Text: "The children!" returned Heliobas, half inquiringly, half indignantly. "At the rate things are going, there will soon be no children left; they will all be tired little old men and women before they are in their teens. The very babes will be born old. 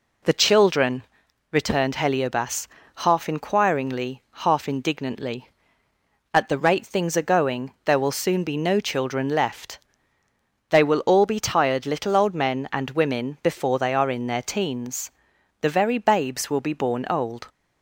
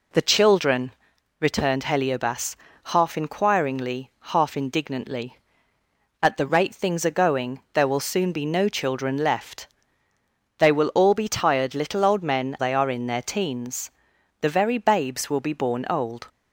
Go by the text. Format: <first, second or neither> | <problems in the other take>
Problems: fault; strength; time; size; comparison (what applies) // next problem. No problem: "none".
first | skips "and women before"; at 12.5 s